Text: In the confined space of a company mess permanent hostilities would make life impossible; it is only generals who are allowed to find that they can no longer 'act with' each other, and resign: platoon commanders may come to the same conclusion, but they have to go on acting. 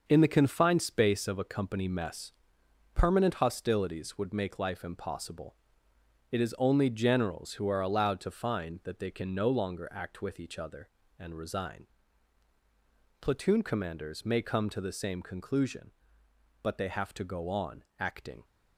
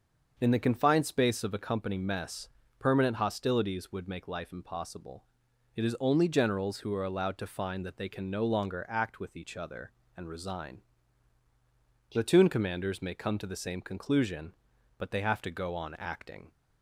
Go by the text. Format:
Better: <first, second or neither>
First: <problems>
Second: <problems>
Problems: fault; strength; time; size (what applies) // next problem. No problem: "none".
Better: second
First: gets quieter; strong; throughout; 7 dB // starts louder than the rest; until 1.0 s; 6 dB // pauses between "mess" and "permanent"; noticeable; at 2.3 s; 0.64 s long // pauses between "on" and "acting"; slight; at 17.8 s; 0.16 s long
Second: starts louder than the rest; until 1.3 s; 6.5 dB // pauses between "mess" and "permanent"; slight; at 2.4 s; 0.30 s long